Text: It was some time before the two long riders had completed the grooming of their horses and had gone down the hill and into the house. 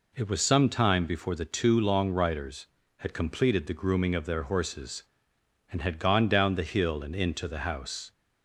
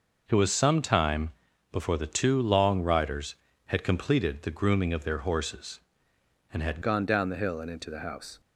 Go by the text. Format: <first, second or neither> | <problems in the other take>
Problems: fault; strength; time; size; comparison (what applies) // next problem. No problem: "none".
first | pauses between "time" and "before"; at 1.2 s; 0.40 s long // changes voice at "gone"; from 6.8 s on; 1.5 s long